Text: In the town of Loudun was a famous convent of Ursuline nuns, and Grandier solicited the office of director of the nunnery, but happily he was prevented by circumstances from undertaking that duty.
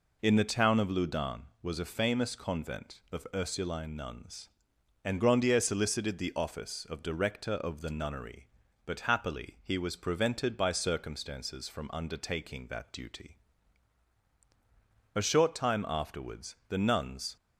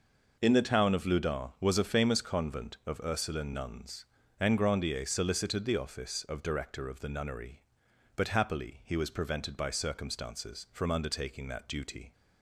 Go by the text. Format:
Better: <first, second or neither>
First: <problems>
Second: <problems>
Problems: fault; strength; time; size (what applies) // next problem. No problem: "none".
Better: second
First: goes on to say "A short time afterwards the nuns"; strong; from 15.1 s on; 2.2 s long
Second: none